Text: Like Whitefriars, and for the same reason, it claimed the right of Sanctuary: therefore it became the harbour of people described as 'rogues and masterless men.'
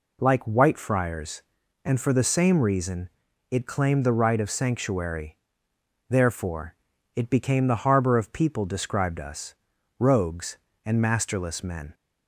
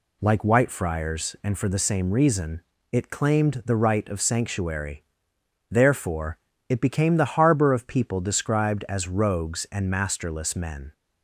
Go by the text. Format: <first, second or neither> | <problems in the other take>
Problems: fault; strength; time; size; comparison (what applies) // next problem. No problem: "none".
second | pauses between "therefore" and "it"; at 6.7 s; 0.40 s long; slight in the second // says "us" for "as"; at 9.1 s